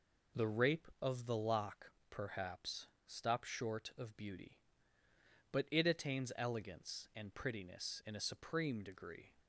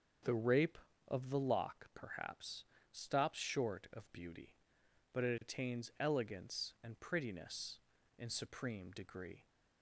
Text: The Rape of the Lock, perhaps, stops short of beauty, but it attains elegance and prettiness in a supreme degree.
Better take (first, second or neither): first